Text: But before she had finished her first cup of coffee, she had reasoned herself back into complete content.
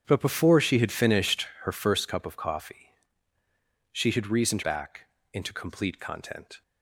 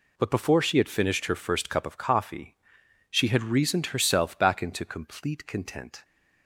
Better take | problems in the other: second | starts louder than the rest; strong; until 1.0 s; 8.5 dB // skips "herself"; at 4.6 s // pauses between "back" and "into"; slight; at 5.0 s; 0.28 s long

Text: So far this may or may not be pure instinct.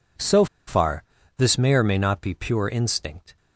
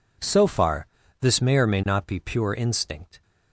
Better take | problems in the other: second | pauses between "So" and "far"; slight; at 0.4 s; 0.22 s long // pauses between "far" and "this"; slight; at 1.0 s; 0.36 s long; slight in the second

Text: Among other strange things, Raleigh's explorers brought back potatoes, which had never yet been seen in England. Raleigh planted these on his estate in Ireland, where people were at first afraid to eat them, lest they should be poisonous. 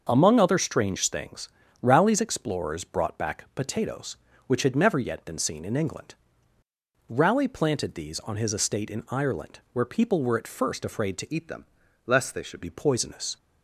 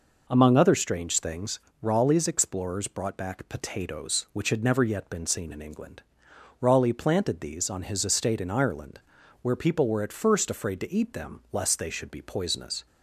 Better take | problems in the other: second | starts louder than the rest; until 1.1 s; 6 dB // changes voice from "eat" to "should"; from 11.3 to 12.5 s; 1.2 s long

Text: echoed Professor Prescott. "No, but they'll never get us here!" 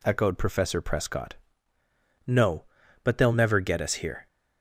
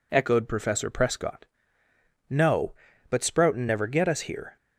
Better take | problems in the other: first | says "sproutin" for "they'll"; at 3.1 s

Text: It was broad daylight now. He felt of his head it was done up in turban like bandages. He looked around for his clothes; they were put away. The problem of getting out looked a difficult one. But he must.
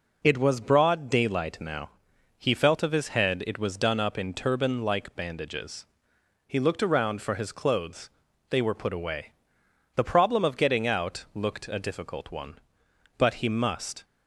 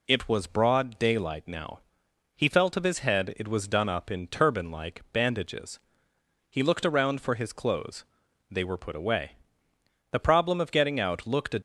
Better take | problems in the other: first | stops before "difficult one But he must"; at 11.5 s

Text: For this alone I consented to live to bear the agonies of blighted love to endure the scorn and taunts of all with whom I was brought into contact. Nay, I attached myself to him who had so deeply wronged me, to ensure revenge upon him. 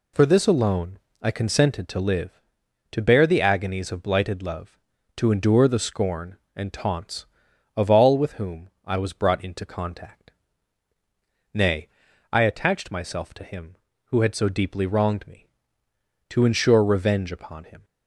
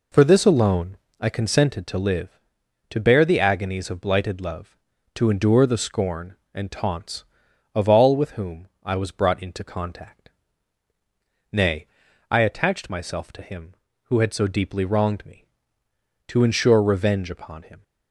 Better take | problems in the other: first | starts louder than the rest; until 1.1 s; 4 dB // pauses between "alone" and "I"; slight; at 0.9 s; 0.20 s long; slight in the first // pauses between "whom" and "I"; slight; at 8.6 s; 0.18 s long; slight in the first

